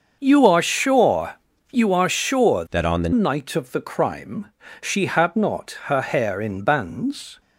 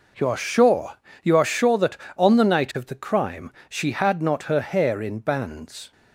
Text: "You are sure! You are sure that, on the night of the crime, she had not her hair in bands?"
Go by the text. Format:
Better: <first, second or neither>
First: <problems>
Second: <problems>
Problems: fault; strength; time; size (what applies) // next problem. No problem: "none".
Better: second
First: starts louder than the rest; until 1.2 s; 6.5 dB // changes voice from "that" to "the"; from 2.7 to 3.1 s; 0.4 s long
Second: none